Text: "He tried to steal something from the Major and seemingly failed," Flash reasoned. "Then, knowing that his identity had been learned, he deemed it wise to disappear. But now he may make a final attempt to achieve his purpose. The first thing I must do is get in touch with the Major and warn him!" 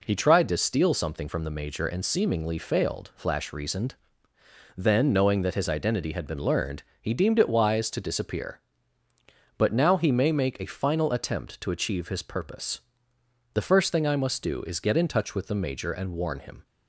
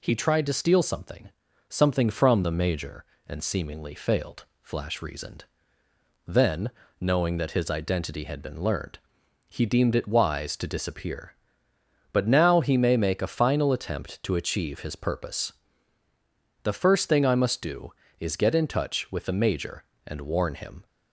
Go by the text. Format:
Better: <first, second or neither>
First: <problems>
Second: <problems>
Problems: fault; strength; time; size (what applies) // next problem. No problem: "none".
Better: first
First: none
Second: says "something" twice; at 1.6 s